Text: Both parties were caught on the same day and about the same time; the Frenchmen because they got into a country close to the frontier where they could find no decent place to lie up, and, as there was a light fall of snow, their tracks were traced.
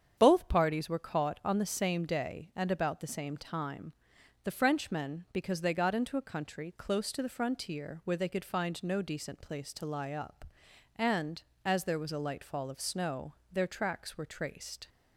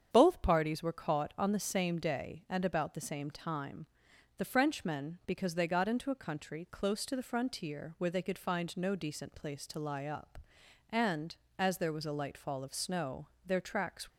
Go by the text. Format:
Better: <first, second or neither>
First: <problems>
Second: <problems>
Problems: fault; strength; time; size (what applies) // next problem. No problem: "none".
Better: first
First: starts louder than the rest; strong; until 1.1 s; 8 dB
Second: starts louder than the rest; strong; until 1.1 s; 8 dB // stops before "were traced"; at 14.0 s